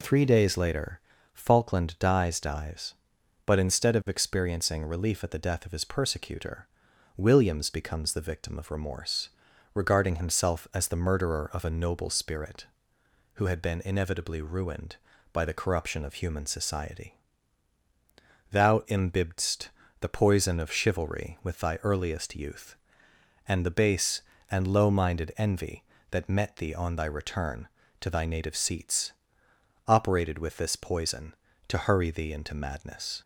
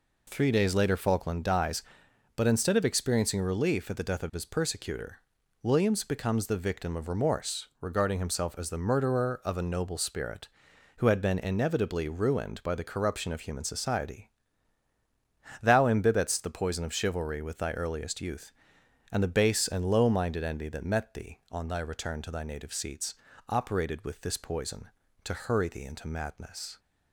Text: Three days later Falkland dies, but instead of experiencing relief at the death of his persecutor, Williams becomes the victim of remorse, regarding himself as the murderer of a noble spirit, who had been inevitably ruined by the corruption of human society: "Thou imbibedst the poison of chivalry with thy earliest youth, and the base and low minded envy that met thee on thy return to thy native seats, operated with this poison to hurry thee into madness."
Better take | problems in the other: second | pauses between "later" and "Falkland"; slight; at 0.9 s; 0.32 s long // says "dies" twice; at 2.3 s // pauses between "imbibedst" and "the"; slight; at 19.6 s; 0.32 s long

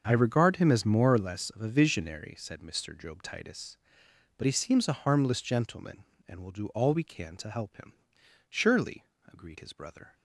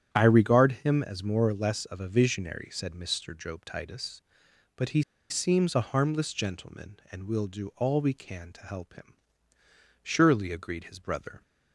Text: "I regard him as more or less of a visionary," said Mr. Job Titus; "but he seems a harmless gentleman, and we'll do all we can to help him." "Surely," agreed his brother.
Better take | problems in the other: first | starts louder than the rest; strong; until 1.1 s; 10 dB; also in the first // pauses between "he" and "seems"; slight; at 5.0 s; 0.28 s long

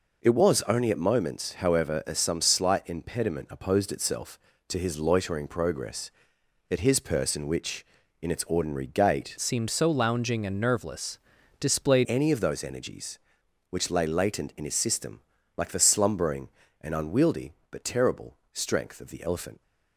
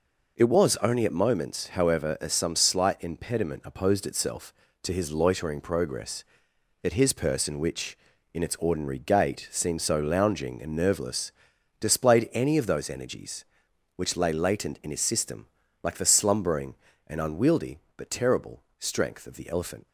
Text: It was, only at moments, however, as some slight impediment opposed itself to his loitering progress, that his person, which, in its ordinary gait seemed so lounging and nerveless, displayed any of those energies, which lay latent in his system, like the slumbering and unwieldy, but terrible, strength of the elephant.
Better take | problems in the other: second | changes voice from "seemed" to "displayed"; from 9.3 to 12.0 s; 2.7 s long

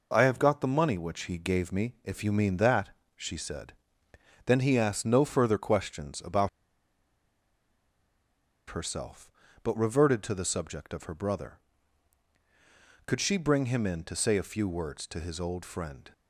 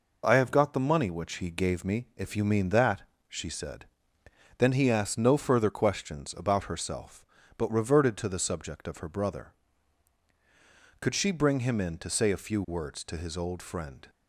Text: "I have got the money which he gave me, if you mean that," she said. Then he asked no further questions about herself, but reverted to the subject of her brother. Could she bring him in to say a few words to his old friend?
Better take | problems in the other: second | pauses between "about" and "herself"; strong; at 6.4 s; 2.2 s long

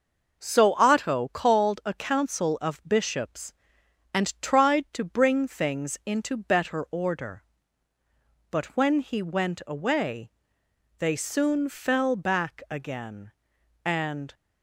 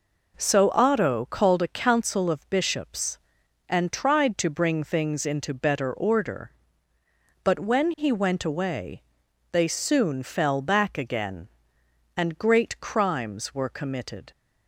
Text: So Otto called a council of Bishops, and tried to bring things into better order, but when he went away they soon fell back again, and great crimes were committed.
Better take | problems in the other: second | pauses between "away" and "they"; noticeable; at 10.2 s; 0.70 s long; noticeable in the second // stops before "great crimes were committed"; at 14.3 s

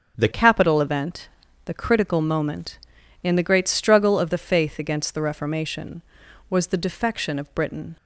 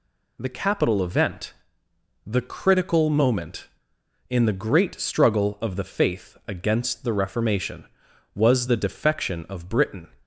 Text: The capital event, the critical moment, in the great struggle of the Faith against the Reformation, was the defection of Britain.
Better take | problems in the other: second | starts louder than the rest; strong; until 1.2 s; 7 dB // changes voice at "capital"; from 0.3 s on; 7.6 s long

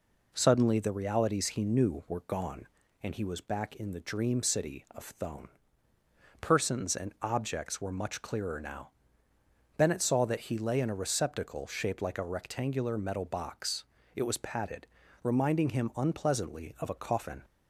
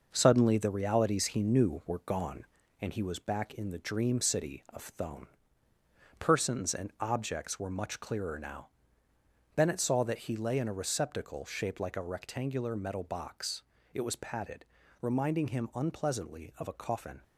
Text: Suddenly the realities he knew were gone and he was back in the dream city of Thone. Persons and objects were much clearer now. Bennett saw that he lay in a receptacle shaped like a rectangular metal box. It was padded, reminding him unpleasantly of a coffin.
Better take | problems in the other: first | gets quieter; noticeable; throughout; 5.5 dB

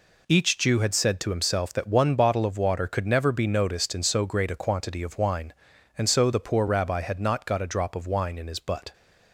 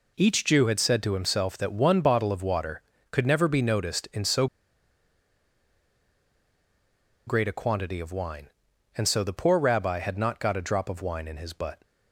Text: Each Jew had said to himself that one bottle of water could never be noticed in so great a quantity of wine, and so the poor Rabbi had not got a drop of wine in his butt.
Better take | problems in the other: first | pauses between "so" and "great"; strong; at 4.4 s; 2.8 s long

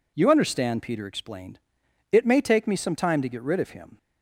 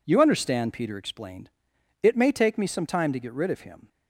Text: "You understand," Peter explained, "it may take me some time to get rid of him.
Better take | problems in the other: first | gets quieter; strong; throughout; 9.5 dB

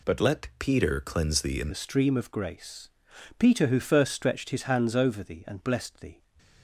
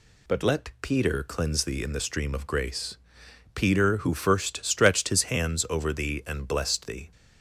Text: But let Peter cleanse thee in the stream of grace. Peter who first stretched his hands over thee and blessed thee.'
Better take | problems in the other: second | changes voice at "the"; from 1.6 s on; 4.6 s long

